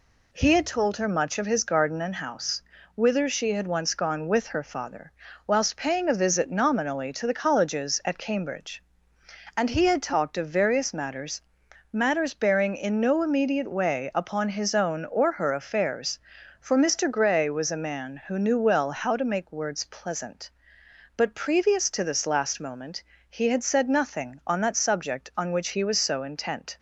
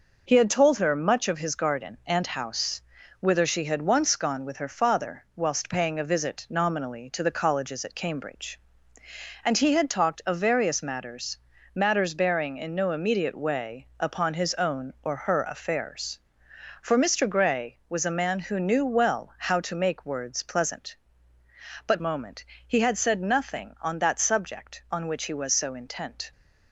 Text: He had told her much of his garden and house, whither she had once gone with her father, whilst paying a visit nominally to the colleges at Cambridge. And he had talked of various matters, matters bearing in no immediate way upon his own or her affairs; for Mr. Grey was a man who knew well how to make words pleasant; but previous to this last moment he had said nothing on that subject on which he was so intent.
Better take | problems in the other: first | skips "previous to this last"; at 21.9 s // pauses between "moment" and "he"; slight; at 22.4 s; 0.22 s long; slight in the first

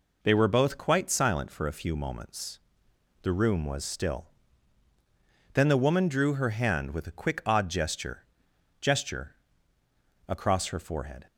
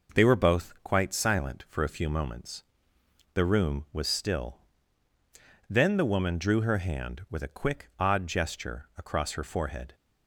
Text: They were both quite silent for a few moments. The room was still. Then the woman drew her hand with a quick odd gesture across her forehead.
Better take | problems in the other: second | says "gesture" twice; at 8.7 s

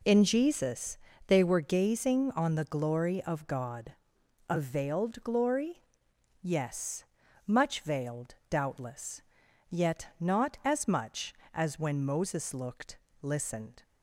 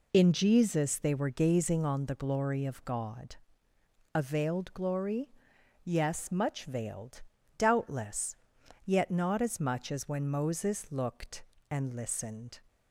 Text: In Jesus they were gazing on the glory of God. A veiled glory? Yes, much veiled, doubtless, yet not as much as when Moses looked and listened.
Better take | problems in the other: second | pauses between "Jesus" and "they"; slight; at 0.9 s; 0.30 s long // skips "and"; at 13.0 s

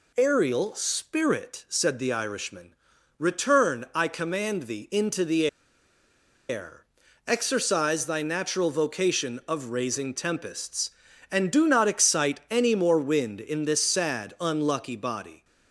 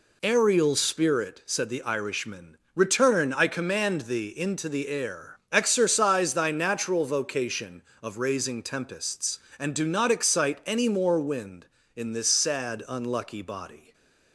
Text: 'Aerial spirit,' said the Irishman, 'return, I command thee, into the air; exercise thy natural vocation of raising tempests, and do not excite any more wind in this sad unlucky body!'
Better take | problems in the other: second | pauses between "the" and "air"; at 5.4 s; 1.0 s long

